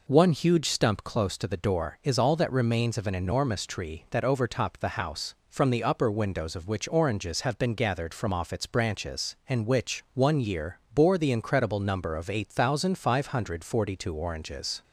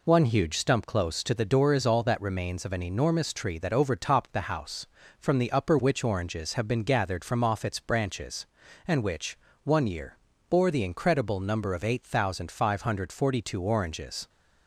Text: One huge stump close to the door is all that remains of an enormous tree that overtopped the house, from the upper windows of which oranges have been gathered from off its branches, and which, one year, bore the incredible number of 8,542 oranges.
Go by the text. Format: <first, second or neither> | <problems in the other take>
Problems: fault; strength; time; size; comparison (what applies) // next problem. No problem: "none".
first | skips "windows of"; at 5.7 s